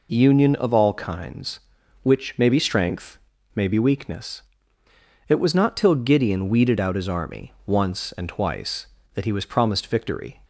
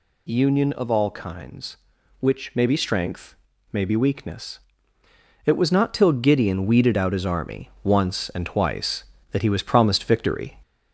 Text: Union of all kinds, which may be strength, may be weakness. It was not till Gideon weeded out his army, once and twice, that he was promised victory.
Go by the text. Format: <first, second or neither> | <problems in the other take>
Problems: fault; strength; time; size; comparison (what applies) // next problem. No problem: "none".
first | gets louder; slight; throughout; 2 dB